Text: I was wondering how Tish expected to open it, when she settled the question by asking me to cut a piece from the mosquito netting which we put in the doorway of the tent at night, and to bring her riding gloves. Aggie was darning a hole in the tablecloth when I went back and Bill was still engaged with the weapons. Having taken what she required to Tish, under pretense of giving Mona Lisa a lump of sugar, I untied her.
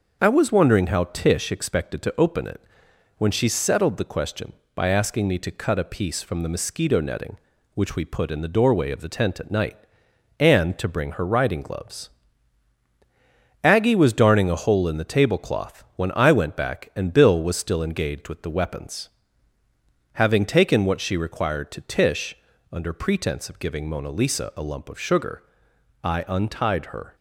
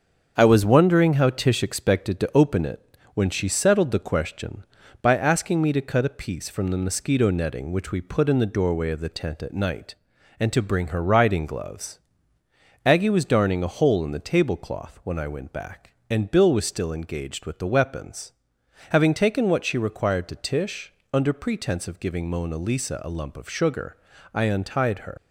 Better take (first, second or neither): first